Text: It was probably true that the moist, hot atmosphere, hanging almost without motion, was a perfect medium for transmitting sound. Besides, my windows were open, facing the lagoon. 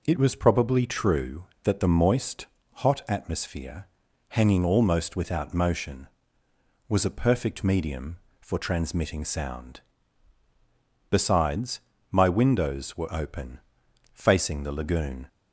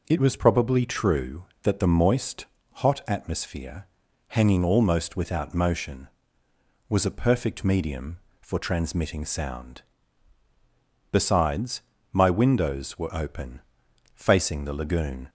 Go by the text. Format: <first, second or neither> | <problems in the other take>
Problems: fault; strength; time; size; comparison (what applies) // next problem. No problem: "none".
neither | none